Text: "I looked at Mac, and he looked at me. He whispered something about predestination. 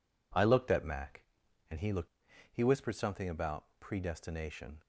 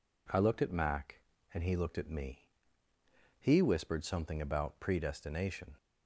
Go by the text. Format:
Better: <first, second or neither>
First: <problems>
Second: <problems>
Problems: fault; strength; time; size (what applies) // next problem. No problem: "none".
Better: second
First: skips "at me"; at 2.3 s // pauses between "about" and "predestination"; slight; at 3.6 s; 0.16 s long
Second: none